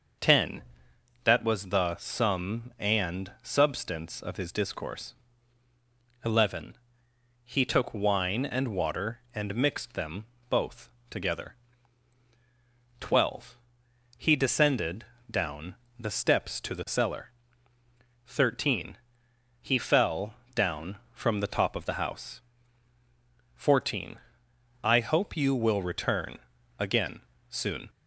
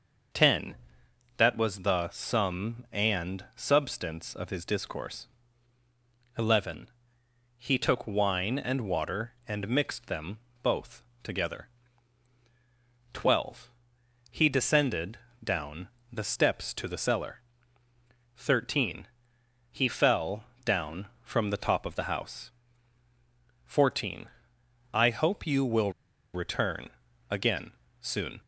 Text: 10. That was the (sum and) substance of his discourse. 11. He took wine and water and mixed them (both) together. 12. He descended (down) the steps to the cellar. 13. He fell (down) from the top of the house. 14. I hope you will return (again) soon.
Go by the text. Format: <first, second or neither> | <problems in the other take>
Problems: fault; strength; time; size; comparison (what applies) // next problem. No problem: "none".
first | starts louder than the rest; until 1.9 s; 6 dB; also in the first // pauses between "will" and "return"; at 25.9 s; 0.42 s long